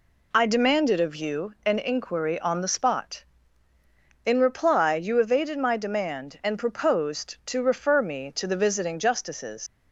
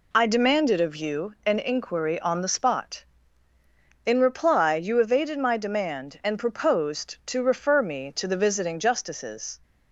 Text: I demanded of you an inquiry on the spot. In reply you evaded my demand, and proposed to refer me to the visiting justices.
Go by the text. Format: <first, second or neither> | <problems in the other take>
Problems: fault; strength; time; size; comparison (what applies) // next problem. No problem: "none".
second | leaves "justices" unfinished; at 9.6 s; 150 ms